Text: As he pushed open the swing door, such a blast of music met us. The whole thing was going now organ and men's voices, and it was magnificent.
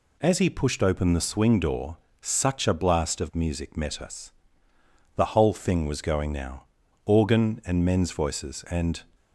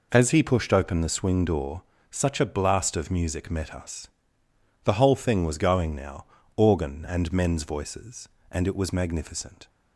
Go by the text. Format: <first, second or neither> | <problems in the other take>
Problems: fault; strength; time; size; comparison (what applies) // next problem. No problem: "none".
second | pauses between "now" and "organ"; at 6.6 s; 0.42 s long; slight in the second // stops before "it was magnificent"; at 9.1 s